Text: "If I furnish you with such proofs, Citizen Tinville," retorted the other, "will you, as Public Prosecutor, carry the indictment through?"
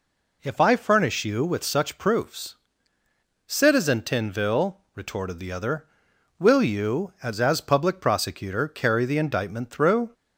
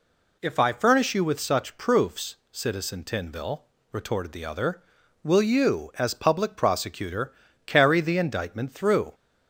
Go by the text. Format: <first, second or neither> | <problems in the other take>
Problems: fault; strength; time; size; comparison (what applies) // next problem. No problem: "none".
second | says "as" twice; at 7.4 s